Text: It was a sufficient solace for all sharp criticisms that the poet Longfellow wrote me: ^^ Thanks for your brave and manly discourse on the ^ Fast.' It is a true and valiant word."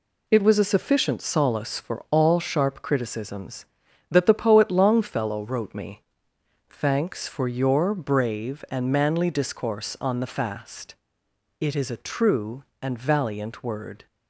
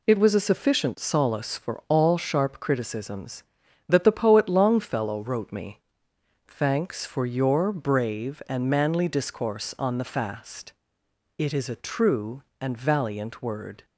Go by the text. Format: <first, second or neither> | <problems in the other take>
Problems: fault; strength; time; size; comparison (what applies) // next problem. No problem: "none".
neither | none